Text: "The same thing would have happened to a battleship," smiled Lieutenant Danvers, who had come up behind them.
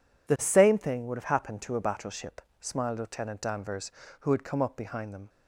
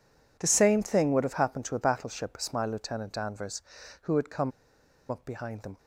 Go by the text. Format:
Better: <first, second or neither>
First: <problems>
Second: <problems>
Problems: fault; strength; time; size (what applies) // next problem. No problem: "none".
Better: first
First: none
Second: pauses between "come" and "up"; noticeable; at 4.5 s; 0.58 s long